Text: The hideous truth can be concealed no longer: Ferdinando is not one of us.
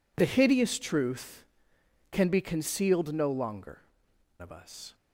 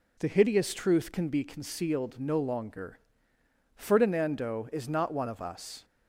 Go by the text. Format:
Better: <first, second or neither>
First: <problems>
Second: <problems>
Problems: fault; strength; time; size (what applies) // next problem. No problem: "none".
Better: second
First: skips "Ferdinando is not one"; at 4.1 s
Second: none